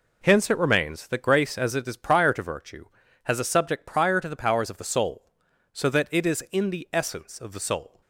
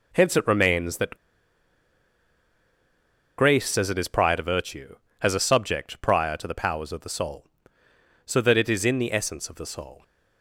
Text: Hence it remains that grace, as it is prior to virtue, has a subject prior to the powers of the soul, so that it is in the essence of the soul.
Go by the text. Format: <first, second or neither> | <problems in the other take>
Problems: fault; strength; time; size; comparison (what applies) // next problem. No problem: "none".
first | pauses between "that" and "grace"; strong; at 1.1 s; 2.2 s long